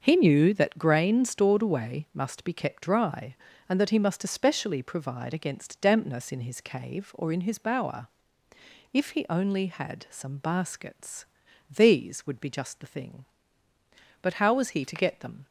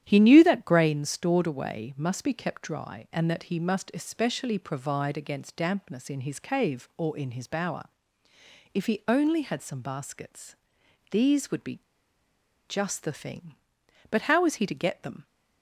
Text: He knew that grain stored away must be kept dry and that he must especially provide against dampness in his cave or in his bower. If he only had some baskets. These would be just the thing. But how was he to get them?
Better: first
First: starts louder than the rest; until 1.0 s; 6.5 dB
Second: starts louder than the rest; strong; until 1.0 s; 10 dB // pauses between "be" and "just"; noticeable; at 11.7 s; 0.89 s long

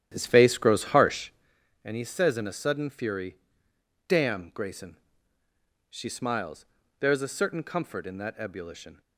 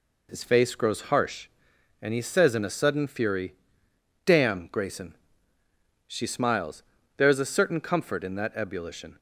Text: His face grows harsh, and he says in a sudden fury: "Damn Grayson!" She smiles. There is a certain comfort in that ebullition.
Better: second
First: starts louder than the rest; strong; until 1.5 s; 11 dB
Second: none

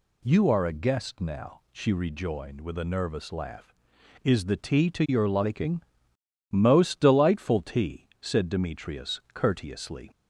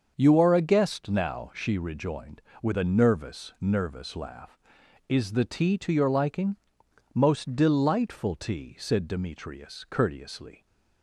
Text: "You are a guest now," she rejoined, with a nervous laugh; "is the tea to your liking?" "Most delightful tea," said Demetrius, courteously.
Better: first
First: none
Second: starts louder than the rest; until 1.1 s; 6.5 dB // says "nervous" twice; at 3.5 s

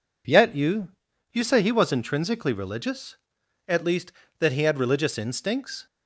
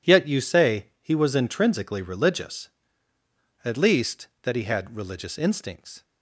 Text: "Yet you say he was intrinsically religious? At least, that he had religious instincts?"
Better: second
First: says "you" twice; at 1.3 s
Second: none

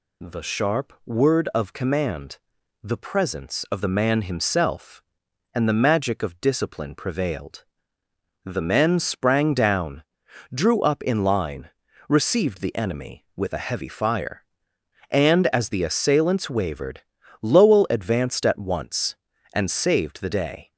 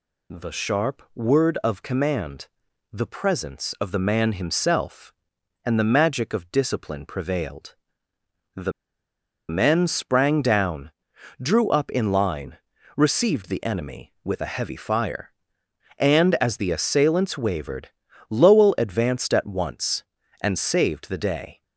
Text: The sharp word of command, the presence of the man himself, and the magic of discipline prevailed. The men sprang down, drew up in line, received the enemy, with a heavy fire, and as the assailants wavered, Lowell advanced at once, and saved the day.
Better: first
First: none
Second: pauses between "The" and "men"; noticeable; at 8.7 s; 0.77 s long

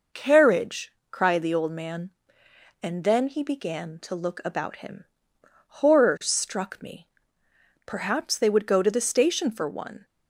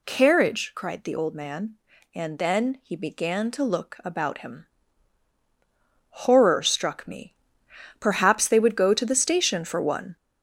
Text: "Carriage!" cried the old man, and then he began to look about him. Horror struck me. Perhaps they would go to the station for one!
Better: first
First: none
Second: gets louder; noticeable; throughout; 5.5 dB

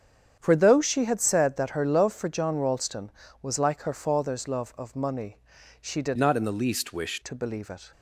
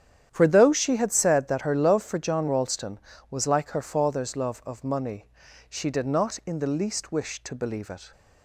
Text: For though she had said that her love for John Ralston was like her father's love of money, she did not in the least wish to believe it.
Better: second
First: starts louder than the rest; strong; until 1.3 s; 8 dB // changes voice from "not" to "wish"; from 6.1 to 7.2 s; 1.1 s long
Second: starts louder than the rest; strong; until 1.3 s; 9.5 dB

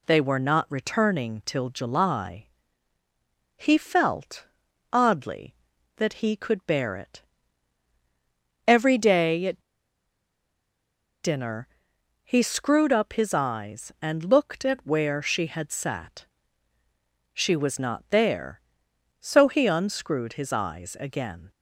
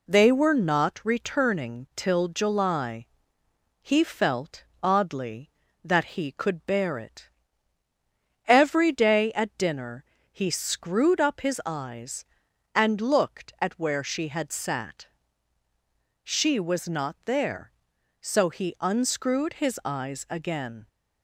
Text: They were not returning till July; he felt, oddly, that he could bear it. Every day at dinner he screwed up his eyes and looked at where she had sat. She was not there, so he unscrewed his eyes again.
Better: second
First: pauses between "at" and "dinner"; strong; at 9.6 s; 1.6 s long // pauses between "dinner" and "he"; noticeable; at 11.6 s; 0.56 s long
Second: pauses between "dinner" and "he"; slight; at 10.0 s; 0.28 s long

